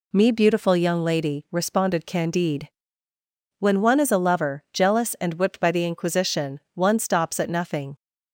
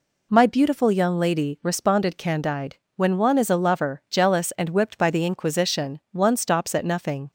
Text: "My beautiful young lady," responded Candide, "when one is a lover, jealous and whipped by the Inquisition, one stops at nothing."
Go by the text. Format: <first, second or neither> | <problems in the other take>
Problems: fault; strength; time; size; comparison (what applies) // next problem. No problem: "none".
second | says "Me" for "My"; at 0.1 s